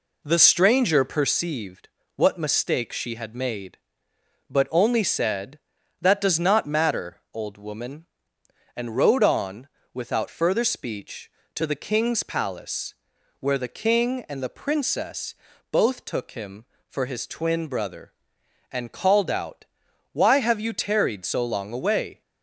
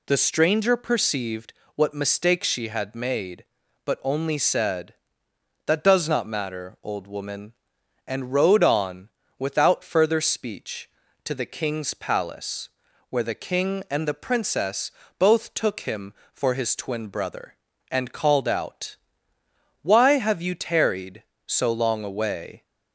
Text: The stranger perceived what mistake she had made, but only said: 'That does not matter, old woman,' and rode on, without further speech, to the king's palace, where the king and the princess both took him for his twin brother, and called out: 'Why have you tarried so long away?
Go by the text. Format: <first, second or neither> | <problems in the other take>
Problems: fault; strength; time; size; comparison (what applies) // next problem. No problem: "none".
second | starts louder than the rest; slight; until 1.4 s; 3 dB // pauses between "perceived" and "what"; slight; at 1.8 s; 0.28 s long; slight in the second // pauses between "princess" and "both"; slight; at 15.3 s; 0.36 s long; slight in the second